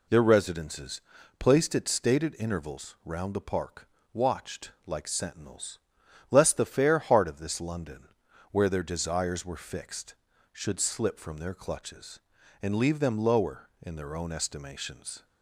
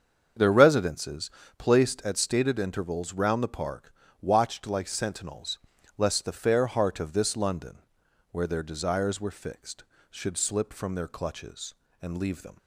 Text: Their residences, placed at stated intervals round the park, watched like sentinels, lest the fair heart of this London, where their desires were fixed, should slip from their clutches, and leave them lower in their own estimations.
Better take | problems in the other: first | starts louder than the rest; until 1.6 s; 7 dB // stops before "lower in their own estimations"; at 12.5 s

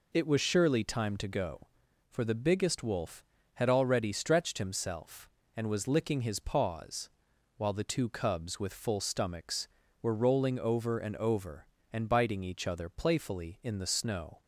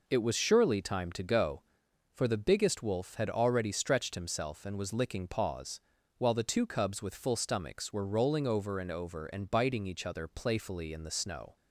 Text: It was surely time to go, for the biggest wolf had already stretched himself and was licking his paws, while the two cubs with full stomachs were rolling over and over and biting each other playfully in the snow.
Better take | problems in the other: first | skips "his"; at 5.2 s

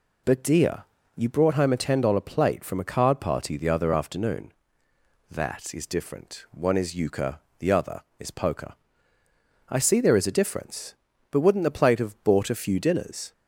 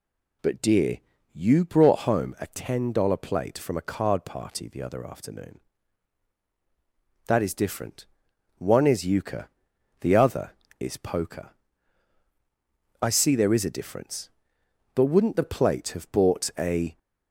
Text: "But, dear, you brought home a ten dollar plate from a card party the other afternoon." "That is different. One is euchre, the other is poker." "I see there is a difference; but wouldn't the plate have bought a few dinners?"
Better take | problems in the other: first | stops before "few dinners"; at 16.9 s

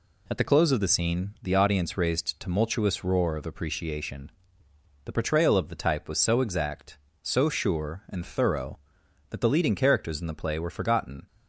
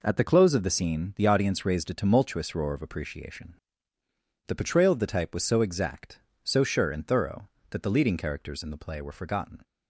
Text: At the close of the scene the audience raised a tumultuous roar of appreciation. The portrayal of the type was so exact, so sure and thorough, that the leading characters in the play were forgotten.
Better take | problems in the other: second | skips "a"; at 2.3 s

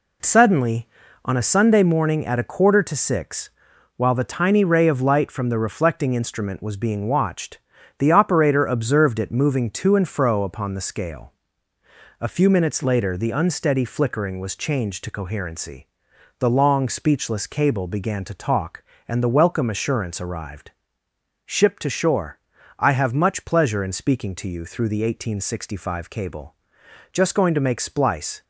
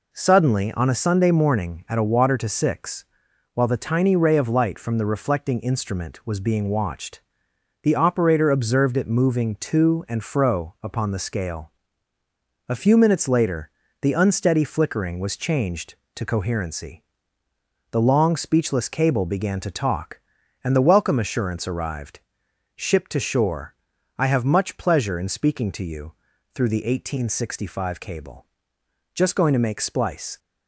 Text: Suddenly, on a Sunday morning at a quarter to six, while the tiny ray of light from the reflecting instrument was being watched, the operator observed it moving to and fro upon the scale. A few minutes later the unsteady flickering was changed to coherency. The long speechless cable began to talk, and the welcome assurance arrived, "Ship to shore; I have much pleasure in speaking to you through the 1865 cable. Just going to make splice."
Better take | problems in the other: first | says "water" for "quarter"; at 2.0 s // pauses between "later" and "the"; slight; at 13.7 s; 0.32 s long // pauses between "you" and "through"; at 26.1 s; 0.40 s long

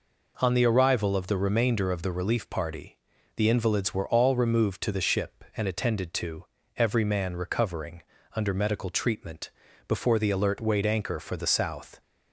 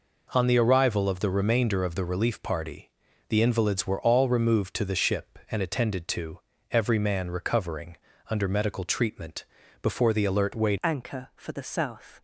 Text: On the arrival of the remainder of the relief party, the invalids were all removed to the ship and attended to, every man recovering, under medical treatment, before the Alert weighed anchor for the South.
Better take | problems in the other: first | changes voice at "anchor"; from 10.8 s on; 1.4 s long

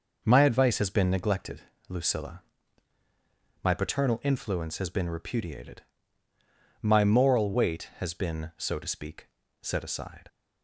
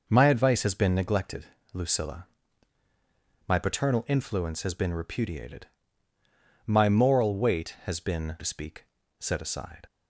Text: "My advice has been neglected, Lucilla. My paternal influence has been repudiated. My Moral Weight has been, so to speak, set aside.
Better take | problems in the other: first | skips "so"; at 8.3 s

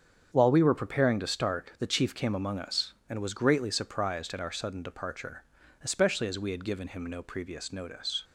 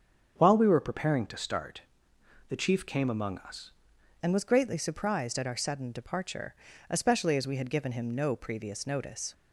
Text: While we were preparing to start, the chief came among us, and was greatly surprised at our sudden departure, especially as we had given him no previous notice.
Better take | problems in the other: first | starts louder than the rest; strong; until 1.4 s; 7 dB; strong in the first // changes voice at "and"; from 4.2 s on; 5.1 s long

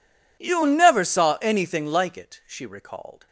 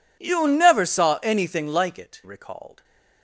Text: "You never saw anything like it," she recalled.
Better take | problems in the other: first | skips "she"; at 2.2 s

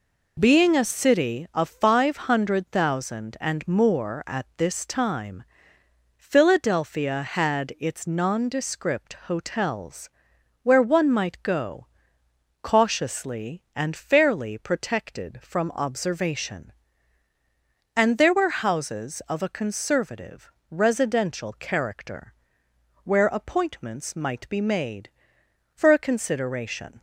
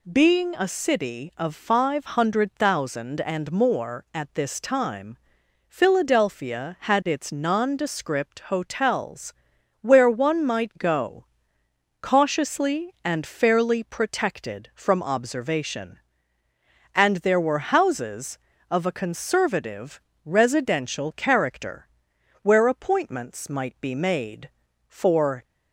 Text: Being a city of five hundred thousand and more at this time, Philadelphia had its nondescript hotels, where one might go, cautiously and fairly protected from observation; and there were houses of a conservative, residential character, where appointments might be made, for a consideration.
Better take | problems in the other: first | stops before "a consideration"; at 25.4 s

